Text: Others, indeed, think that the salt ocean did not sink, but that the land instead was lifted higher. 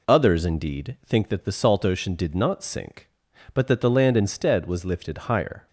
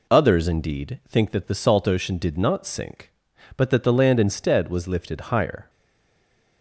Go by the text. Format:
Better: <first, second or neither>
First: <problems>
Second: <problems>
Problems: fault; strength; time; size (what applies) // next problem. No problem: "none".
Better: first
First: none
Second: stays silent after the last word; from 5.6 s on; 1.0 s long